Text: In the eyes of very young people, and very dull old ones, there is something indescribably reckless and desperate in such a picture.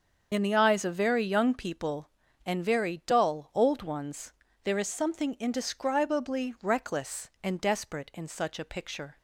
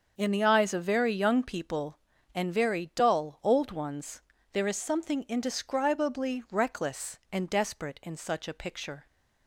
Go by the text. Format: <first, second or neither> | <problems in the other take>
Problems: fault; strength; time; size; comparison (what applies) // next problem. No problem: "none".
second | loses the start of "In"; at 0.3 s; 45 ms // starts louder than the rest; until 1.3 s; 6.5 dB; also in the second